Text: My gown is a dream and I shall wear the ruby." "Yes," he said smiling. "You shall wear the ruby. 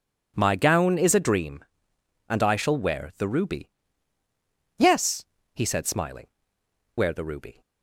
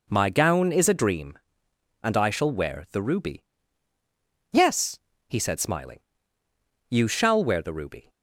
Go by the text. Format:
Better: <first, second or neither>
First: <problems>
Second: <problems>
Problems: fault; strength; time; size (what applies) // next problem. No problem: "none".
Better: second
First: skips "You shall"; at 6.6 s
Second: none